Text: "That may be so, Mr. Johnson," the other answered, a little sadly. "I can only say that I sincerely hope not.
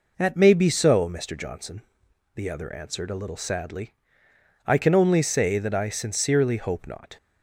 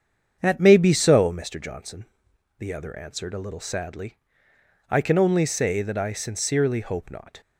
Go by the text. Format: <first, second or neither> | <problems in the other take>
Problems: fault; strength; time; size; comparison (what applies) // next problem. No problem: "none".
first | starts louder than the rest; strong; until 1.5 s; 7.5 dB